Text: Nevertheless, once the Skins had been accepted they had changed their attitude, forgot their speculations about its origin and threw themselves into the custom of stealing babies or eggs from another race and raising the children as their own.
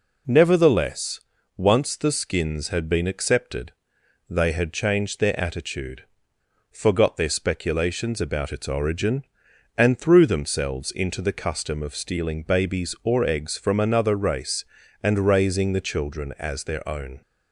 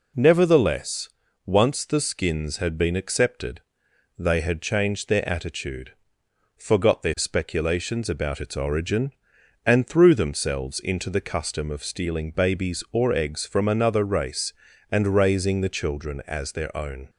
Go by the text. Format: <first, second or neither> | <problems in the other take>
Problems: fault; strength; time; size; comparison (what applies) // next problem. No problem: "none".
neither | pauses between "accepted" and "they"; noticeable; the same in both